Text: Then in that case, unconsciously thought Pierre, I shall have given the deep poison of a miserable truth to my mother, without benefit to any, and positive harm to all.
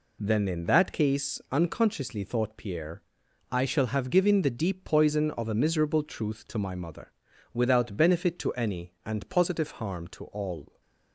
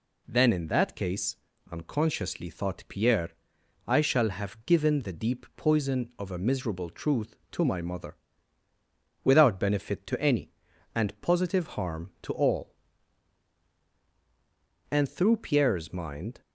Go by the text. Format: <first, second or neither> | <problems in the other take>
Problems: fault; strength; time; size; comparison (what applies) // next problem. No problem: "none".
first | goes on to say "And through Pierre's mind"; from 14.9 s on; 1.5 s long